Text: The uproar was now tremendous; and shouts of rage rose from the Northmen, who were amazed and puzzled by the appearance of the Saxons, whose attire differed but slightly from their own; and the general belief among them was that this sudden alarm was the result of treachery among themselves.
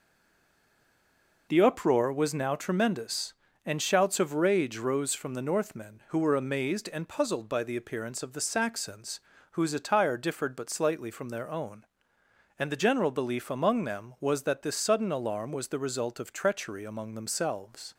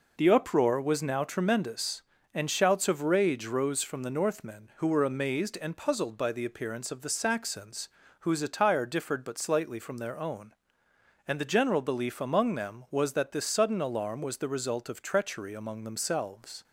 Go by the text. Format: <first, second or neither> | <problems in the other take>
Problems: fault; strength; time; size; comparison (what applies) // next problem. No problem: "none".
second | stays silent before the first word; noticeable; until 1.4 s; 1.4 s long